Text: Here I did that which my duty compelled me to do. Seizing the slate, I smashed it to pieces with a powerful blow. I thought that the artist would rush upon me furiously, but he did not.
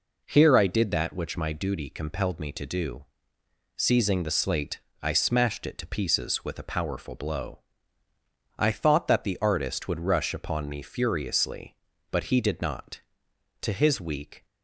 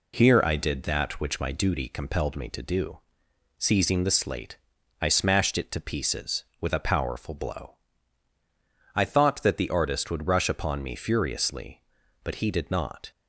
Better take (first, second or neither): second